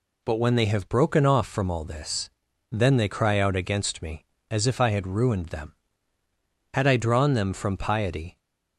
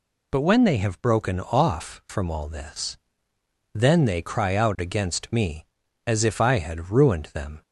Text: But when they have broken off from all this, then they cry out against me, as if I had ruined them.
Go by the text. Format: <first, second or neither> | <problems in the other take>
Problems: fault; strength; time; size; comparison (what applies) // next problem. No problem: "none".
second | goes on to say "Had I drawn them from piety"; from 6.7 s on; 1.6 s long